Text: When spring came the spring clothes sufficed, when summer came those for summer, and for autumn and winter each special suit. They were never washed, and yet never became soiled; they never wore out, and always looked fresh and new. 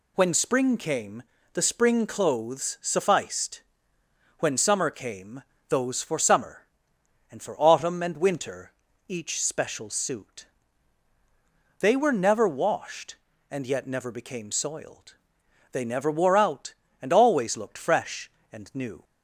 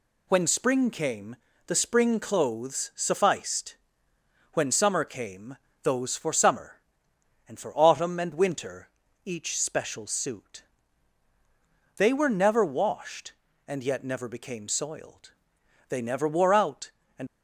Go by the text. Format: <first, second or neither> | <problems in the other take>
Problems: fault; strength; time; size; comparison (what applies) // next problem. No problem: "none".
first | pauses between "came" and "the"; slight; at 1.3 s; 0.30 s long; slight in the first // pauses between "came" and "those"; slight; at 5.5 s; 0.28 s long; slight in the first // pauses between "winter" and "each"; slight; at 8.9 s; 0.34 s long; slight in the first // stops before "always looked fresh and new"; at 17.2 s